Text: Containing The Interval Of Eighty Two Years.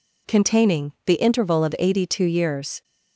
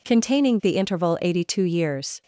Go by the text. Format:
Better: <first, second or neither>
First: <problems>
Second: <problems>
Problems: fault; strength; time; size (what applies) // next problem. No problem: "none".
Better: first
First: none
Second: skips "Of"; at 1.1 s